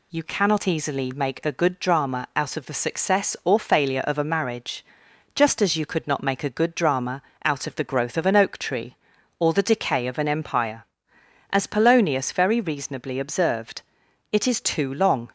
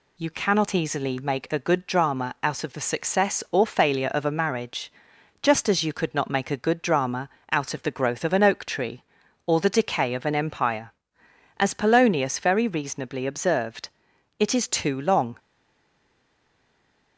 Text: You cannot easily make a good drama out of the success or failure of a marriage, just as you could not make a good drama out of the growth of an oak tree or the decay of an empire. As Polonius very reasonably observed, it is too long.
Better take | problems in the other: first | pauses between "drama" and "out"; slight; at 7.2 s; 0.22 s long; slight in the first // stays silent after the last word; noticeable; from 15.3 s on; 1.8 s long

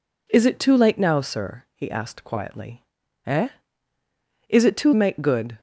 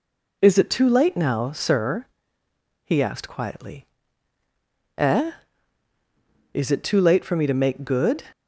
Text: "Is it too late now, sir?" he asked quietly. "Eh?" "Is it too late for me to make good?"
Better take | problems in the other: second | skips "late for me to"; at 4.9 s

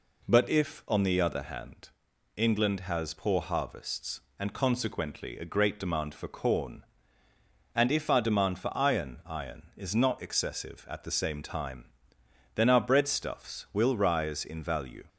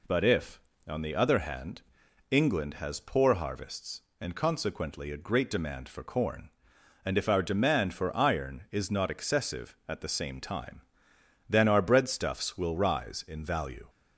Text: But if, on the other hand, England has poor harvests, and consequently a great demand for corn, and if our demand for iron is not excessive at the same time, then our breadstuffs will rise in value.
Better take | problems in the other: second | says "iron" twice; at 9.2 s

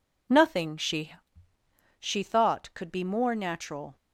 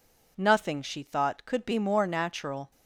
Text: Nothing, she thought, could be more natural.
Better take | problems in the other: second | says "she" twice; at 2.0 s

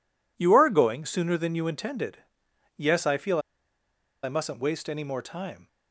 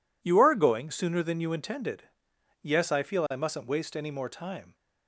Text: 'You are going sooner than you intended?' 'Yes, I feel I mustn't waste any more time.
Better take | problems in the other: second | pauses between "feel" and "I"; noticeable; at 3.3 s; 0.83 s long

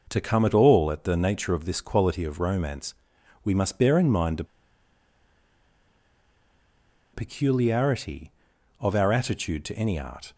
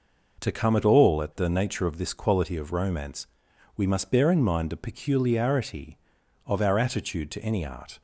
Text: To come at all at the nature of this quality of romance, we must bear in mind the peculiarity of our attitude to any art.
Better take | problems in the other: second | pauses between "the" and "peculiarity"; strong; at 4.4 s; 2.6 s long

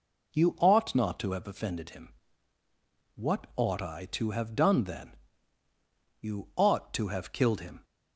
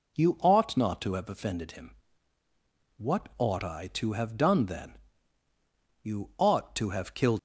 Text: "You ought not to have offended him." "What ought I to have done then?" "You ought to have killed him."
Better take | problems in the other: first | stops before "him"; at 7.3 s

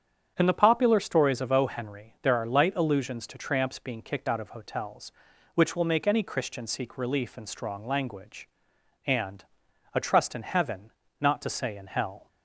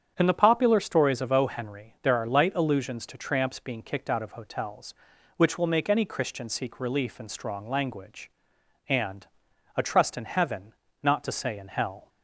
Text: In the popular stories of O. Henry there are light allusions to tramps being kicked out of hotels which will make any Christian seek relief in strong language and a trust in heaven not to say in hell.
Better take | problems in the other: neither | starts louder than the rest; strong; the same in both // pauses between "and" and "a"; noticeable; the same in both // pauses between "heaven" and "not"; slight; the same in both

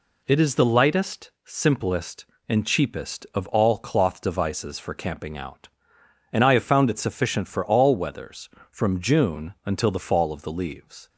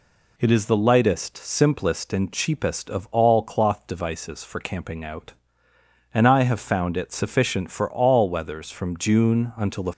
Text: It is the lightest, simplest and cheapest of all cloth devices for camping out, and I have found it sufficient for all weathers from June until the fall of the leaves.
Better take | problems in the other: first | stops before "fall of the leaves"; at 9.9 s

